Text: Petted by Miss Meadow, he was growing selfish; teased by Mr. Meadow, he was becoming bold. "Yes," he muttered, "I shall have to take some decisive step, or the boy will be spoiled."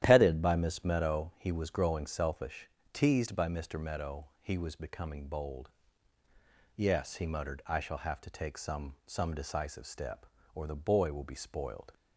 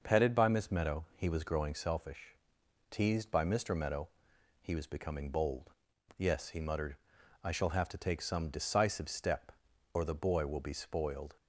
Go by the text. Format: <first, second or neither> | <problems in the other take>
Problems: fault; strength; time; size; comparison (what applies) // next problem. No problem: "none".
second | starts louder than the rest; strong; until 1.0 s; 11 dB // says "some" twice; at 9.0 s